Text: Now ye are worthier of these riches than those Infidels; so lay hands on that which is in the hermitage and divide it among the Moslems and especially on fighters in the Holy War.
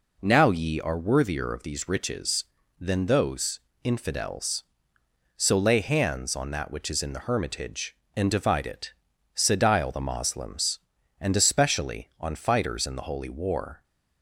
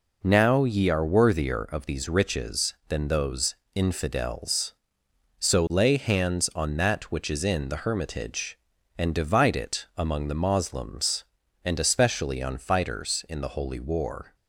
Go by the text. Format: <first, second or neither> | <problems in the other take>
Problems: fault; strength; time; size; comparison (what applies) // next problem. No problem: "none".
second | pauses between "those" and "Infidels"; slight; at 3.6 s; 0.24 s long; slight in the second // says "sedile" for "among"; at 9.3 s